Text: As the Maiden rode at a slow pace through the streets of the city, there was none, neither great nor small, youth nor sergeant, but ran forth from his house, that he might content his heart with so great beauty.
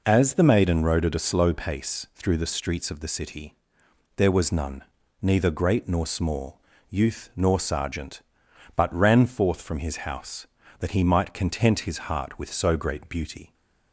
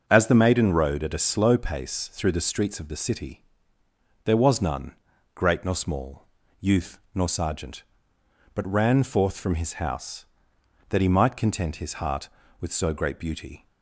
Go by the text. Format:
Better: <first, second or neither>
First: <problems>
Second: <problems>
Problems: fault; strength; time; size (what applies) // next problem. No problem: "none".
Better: first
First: none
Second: starts louder than the rest; until 1.0 s; 6.5 dB // skips "neither"; at 5.1 s